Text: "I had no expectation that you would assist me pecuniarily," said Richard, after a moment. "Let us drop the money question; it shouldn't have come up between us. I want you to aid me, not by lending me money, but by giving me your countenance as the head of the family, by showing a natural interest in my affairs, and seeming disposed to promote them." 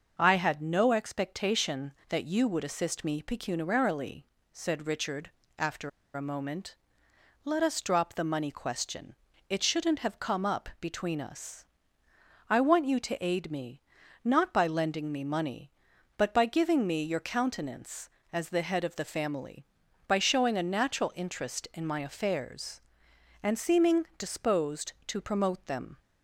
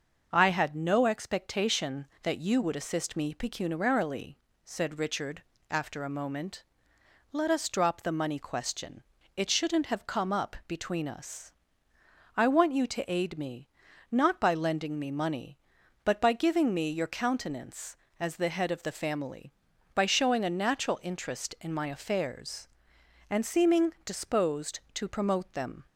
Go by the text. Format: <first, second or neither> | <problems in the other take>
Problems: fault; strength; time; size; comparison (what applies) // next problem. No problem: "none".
second | starts louder than the rest; until 1.1 s; 6 dB; also in the second // pauses between "after" and "a"; slight; at 5.8 s; 0.25 s long